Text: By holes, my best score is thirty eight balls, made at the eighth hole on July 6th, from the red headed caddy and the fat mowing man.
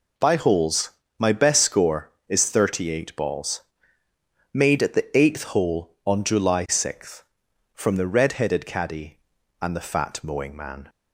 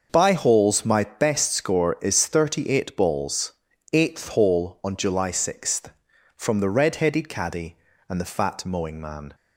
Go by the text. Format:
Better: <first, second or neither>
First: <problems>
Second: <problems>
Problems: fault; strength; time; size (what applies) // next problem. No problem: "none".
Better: first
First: none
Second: starts louder than the rest; until 1.1 s; 6.5 dB // skips "made at the"; at 3.7 s